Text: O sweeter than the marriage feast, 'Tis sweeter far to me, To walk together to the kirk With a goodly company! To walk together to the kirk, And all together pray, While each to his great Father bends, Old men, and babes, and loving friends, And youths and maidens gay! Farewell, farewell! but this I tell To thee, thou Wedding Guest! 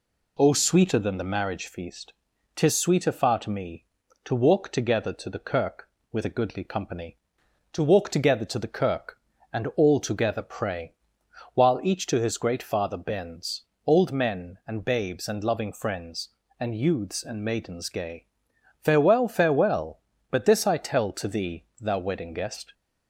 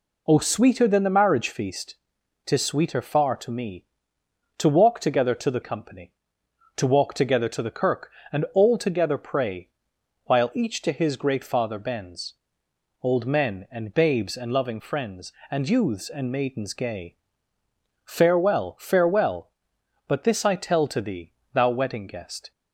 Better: first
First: none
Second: skips "kirk With a goodly"; at 5.6 s

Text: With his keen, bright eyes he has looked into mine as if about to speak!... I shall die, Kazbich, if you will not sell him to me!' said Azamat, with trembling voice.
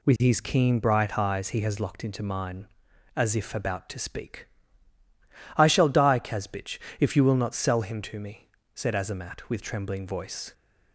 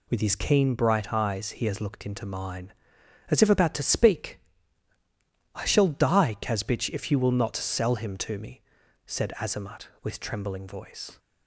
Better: second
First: says "locked" for "looked"; at 1.7 s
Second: none

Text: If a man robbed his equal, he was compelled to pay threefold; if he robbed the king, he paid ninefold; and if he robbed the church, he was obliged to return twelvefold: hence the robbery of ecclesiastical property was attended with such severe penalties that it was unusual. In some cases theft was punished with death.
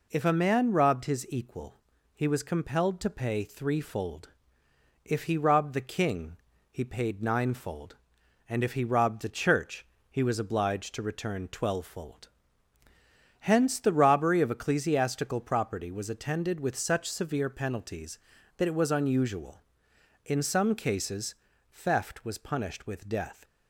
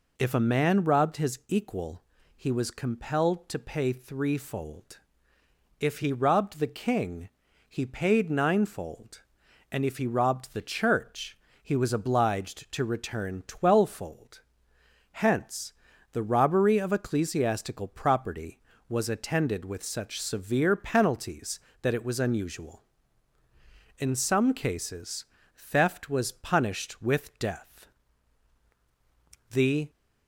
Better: first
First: pauses between "cases" and "theft"; at 21.3 s; 0.38 s long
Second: pauses between "hence" and "the"; at 15.7 s; 0.38 s long // pauses between "cases" and "theft"; slight; at 25.2 s; 0.28 s long // goes on to say "The"; slight; from 29.4 s on; 0.40 s long

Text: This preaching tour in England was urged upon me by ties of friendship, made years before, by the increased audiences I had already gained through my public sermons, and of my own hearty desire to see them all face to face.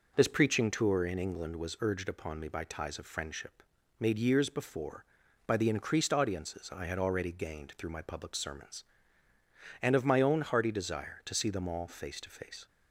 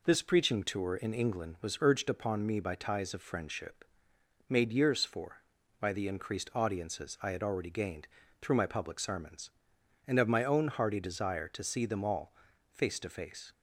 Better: first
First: none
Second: says "for" for "before"; at 5.0 s // pauses between "gained" and "through"; slight; at 8.0 s; 0.32 s long // pauses between "all" and "face"; at 12.3 s; 0.38 s long

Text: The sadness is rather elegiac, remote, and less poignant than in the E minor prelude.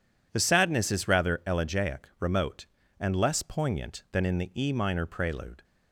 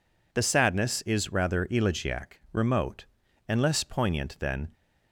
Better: first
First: none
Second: stops before "in the E minor prelude"; at 4.7 s

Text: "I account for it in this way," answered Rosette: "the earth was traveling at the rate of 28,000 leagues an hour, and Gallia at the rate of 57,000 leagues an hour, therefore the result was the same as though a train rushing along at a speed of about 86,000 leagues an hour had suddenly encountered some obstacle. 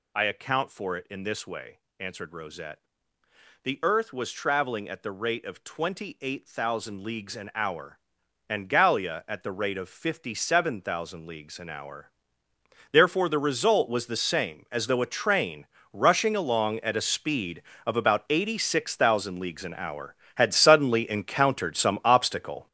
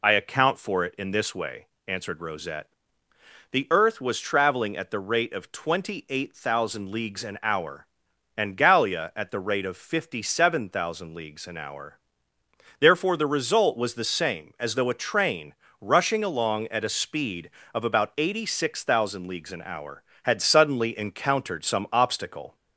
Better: second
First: gets louder; strong; throughout; 10 dB // pauses between "train" and "rushing"; slight; at 15.6 s; 0.26 s long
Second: pauses between "train" and "rushing"; slight; at 15.5 s; 0.26 s long

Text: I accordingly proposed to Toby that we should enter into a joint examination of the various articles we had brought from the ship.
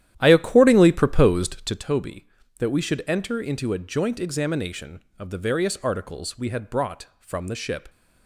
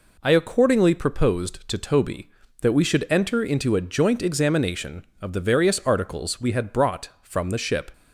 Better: second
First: starts louder than the rest; strong; until 1.9 s; 11.5 dB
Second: none

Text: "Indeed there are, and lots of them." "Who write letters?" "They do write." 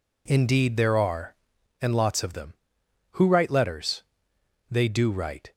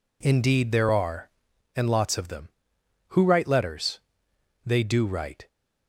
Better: neither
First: none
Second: none

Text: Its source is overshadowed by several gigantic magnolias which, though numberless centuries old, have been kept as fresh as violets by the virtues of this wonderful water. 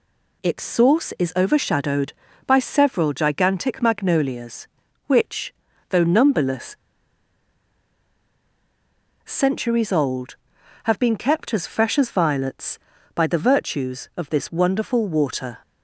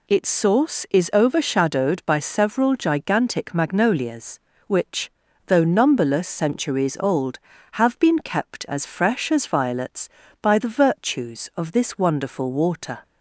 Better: second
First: pauses between "numberless" and "centuries"; strong; at 6.7 s; 2.4 s long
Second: none

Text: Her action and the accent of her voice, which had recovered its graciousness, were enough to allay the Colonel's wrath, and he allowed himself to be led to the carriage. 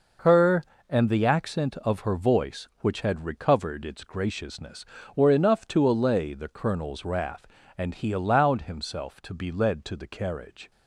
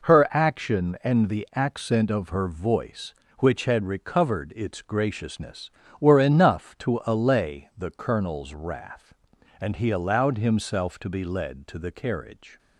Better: second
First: skips "action"; at 0.7 s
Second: none

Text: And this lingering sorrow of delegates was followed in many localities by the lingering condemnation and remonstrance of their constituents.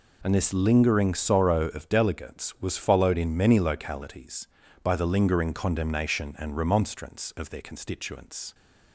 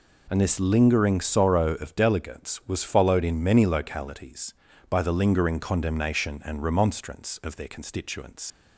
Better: first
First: none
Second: leaves "constituents" unfinished; at 8.5 s; 105 ms

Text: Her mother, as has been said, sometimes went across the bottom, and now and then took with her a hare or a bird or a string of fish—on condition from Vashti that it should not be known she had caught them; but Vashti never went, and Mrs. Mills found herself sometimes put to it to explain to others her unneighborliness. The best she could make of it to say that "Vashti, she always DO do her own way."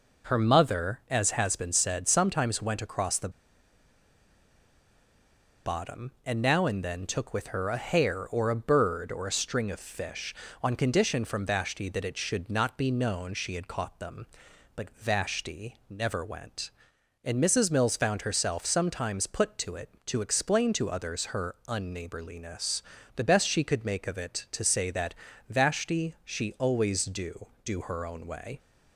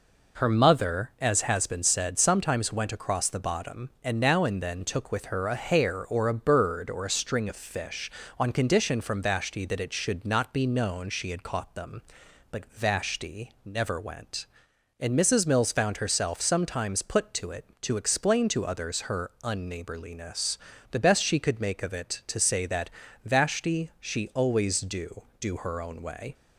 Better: second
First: pauses between "the" and "bottom"; strong; at 3.2 s; 2.3 s long // pauses between "that" and "Vashti"; slight; at 25.1 s; 0.34 s long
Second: pauses between "that" and "Vashti"; slight; at 22.8 s; 0.34 s long

